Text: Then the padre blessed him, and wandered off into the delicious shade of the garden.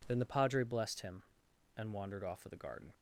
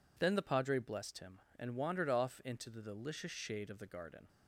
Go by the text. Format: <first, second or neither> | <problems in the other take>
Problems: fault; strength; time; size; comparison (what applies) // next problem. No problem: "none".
second | skips "into the delicious shade"; at 2.4 s